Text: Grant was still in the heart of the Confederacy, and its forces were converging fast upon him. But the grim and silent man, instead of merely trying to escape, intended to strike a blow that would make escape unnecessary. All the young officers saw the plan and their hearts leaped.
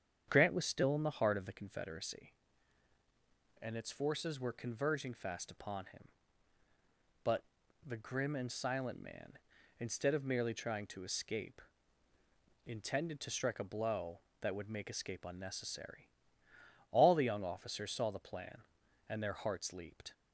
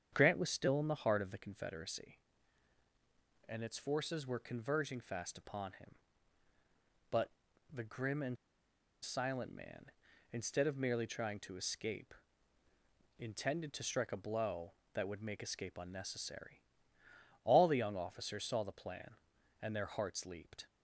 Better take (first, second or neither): first